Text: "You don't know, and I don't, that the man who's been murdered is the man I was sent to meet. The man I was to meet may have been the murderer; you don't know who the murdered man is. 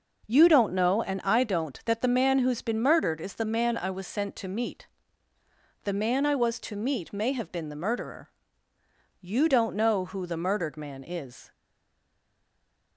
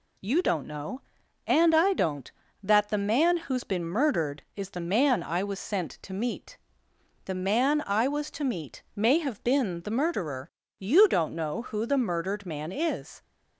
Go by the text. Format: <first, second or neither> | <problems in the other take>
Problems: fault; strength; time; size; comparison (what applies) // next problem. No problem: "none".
second | stays silent after the last word; noticeable; from 11.5 s on; 1.4 s long